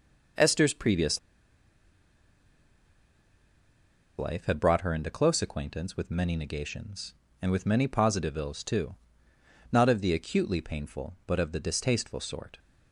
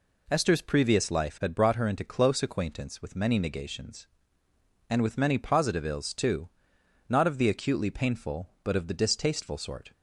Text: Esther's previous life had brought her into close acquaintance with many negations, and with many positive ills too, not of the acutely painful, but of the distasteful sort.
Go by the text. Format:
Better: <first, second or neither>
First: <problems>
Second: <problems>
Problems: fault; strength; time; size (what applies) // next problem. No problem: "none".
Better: second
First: pauses between "previous" and "life"; strong; at 1.1 s; 2.9 s long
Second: none